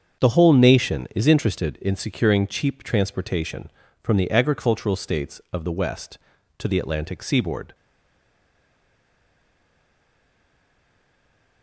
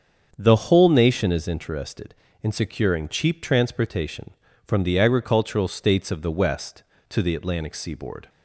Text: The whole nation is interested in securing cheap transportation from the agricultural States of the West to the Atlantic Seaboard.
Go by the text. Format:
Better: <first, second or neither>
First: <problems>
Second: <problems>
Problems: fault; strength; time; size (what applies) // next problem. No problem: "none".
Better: second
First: starts louder than the rest; until 1.2 s; 7 dB // stays silent after the last word; strong; from 7.7 s on; 3.9 s long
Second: starts louder than the rest; until 1.3 s; 7 dB